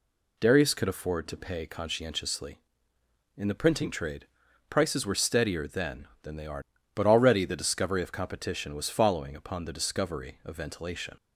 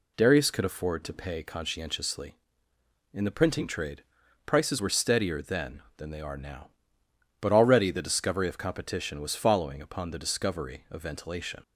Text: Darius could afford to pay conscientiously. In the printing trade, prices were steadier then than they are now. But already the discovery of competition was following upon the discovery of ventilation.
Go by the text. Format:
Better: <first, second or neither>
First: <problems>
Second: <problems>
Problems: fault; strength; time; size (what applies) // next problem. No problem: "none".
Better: second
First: skips "now"; at 6.7 s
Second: none